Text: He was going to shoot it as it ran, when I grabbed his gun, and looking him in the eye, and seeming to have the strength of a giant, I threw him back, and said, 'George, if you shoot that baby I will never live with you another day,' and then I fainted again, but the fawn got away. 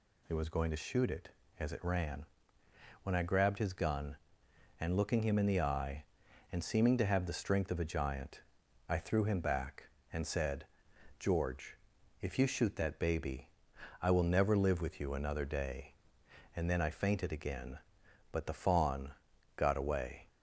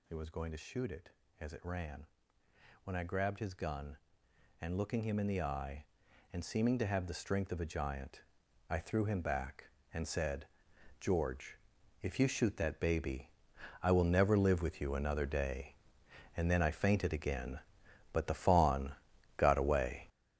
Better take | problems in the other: first | gets louder; strong; throughout; 9.5 dB // pauses between "baby" and "I"; noticeable; at 13.3 s; 0.52 s long; noticeable in the first // pauses between "fawn" and "got"; noticeable; at 18.9 s; 0.46 s long; noticeable in the first

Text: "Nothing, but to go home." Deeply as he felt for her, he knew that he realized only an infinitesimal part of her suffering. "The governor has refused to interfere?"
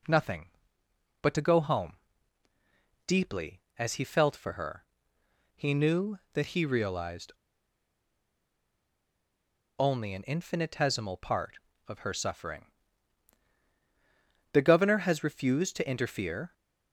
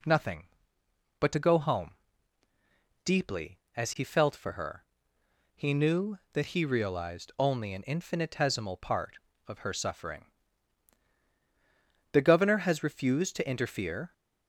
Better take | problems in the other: second | pauses between "realized" and "only"; strong; at 7.3 s; 2.4 s long

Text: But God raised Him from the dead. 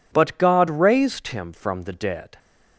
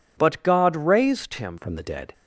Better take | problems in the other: first | changes voice at "from"; from 1.5 s on; 0.6 s long

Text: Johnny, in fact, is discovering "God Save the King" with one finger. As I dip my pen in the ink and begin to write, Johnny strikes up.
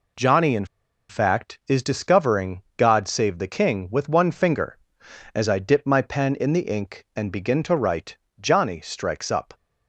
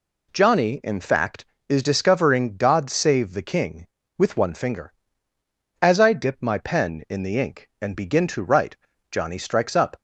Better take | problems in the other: second | pauses between "in" and "fact"; at 0.6 s; 0.45 s long // pauses between "discovering" and "God"; slight; at 2.6 s; 0.16 s long

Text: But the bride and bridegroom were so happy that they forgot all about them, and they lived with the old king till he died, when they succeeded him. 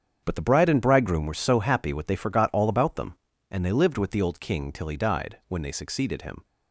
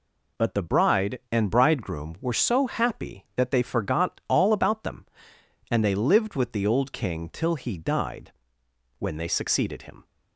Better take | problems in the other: second | starts louder than the rest; strong; until 1.2 s; 8 dB // says "what" for "that"; at 1.9 s

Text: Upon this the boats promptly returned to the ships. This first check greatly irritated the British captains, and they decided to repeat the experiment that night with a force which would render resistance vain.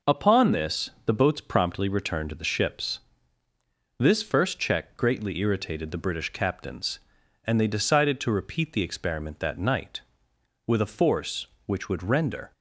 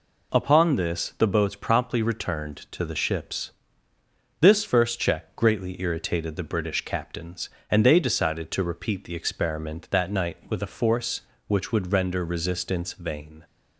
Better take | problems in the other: second | stops before "resistance vain"; at 12.5 s

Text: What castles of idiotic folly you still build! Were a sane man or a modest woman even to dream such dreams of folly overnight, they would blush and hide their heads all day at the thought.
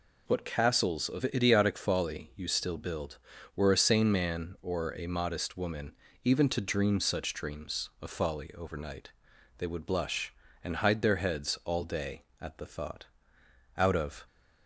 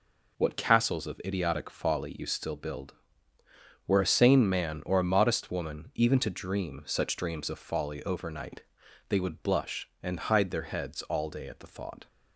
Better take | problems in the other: second | pauses between "woman" and "even"; slight; at 5.9 s; 0.32 s long // goes on to say "Out of"; slight; from 13.7 s on; 0.48 s long

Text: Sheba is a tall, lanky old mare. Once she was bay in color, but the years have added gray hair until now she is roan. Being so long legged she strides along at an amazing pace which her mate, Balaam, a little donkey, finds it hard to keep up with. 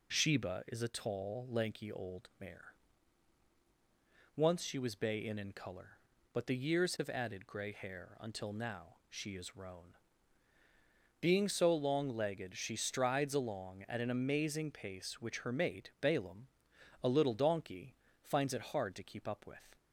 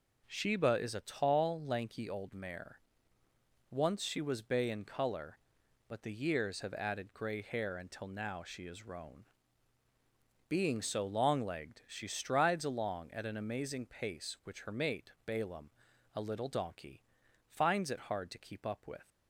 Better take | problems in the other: second | says "in" twice; at 5.3 s

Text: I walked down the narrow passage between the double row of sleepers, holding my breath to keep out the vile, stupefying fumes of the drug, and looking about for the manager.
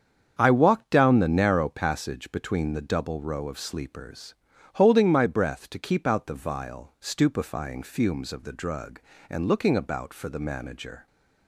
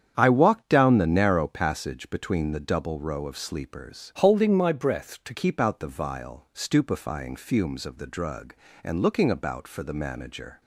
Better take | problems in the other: first | starts louder than the rest; strong; until 1.1 s; 8.5 dB; strong in the first // changes voice from "holding" to "to"; from 4.1 to 5.3 s; 1.2 s long

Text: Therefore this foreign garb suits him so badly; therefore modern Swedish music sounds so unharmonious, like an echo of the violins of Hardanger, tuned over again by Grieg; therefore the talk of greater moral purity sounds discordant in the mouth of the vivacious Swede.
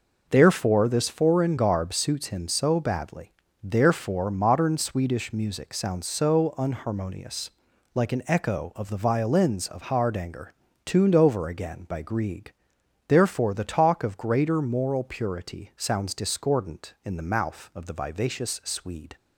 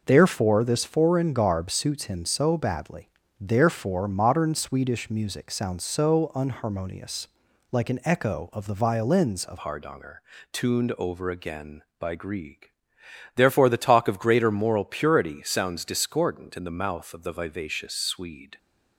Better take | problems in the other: first | changes voice at "Hardanger"; from 9.5 s on; 9.0 s long

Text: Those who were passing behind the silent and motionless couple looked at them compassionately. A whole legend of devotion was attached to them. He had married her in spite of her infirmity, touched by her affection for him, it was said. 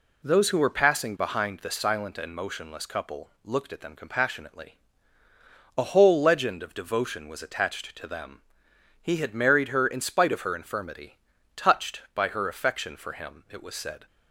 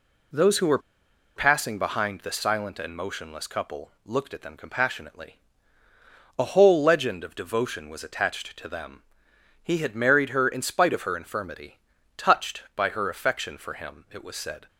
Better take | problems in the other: first | pauses between "were" and "passing"; noticeable; at 0.7 s; 0.57 s long

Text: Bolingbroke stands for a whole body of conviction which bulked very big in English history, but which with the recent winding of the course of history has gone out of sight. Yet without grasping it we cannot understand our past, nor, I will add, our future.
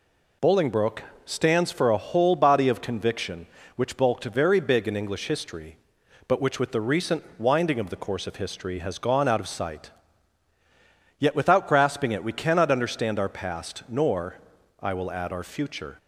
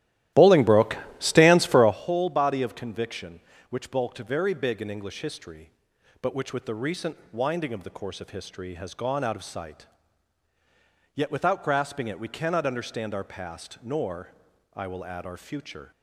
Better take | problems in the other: first | starts louder than the rest; strong; until 2.1 s; 14 dB // pauses between "Bolingbroke" and "stands"; slight; at 0.9 s; 0.22 s long; slight in the first

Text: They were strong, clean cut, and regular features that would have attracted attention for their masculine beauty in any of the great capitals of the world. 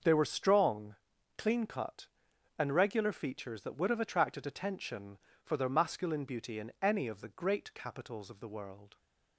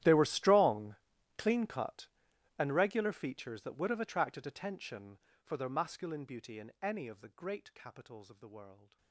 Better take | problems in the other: first | gets quieter; strong; throughout; 23 dB // starts louder than the rest; strong; until 1.4 s; 12.5 dB; noticeable in the first

